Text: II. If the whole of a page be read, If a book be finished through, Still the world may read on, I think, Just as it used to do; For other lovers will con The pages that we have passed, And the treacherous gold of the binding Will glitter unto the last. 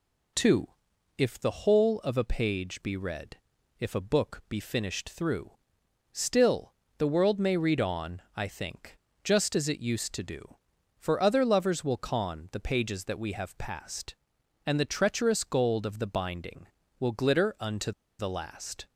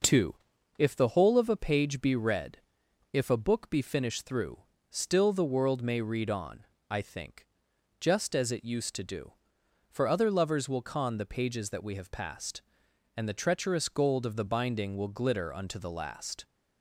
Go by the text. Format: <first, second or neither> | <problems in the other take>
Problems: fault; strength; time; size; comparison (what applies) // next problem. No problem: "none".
second | pauses between "Still" and "the"; slight; at 6.7 s; 0.24 s long // pauses between "unto" and "the"; slight; at 17.9 s; 0.28 s long